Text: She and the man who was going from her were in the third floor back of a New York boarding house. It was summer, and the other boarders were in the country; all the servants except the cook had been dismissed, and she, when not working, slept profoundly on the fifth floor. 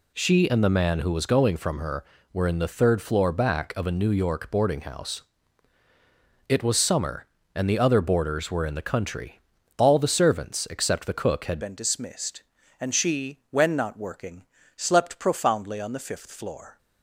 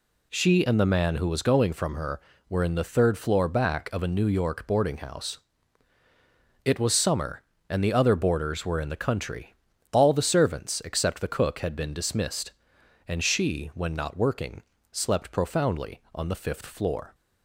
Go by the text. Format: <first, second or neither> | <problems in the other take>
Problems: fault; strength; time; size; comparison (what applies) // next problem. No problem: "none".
second | changes voice at "been"; from 11.6 s on; 5.1 s long